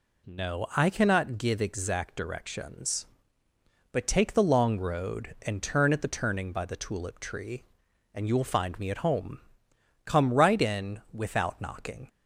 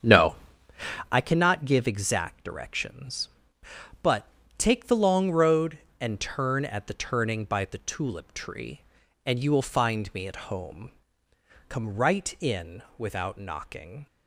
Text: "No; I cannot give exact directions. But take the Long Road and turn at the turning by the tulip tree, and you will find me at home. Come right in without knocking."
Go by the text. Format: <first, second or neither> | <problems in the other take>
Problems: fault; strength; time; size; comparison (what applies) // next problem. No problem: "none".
first | starts louder than the rest; strong; until 1.2 s; 8 dB // pauses between "But" and "take"; slight; at 4.2 s; 0.30 s long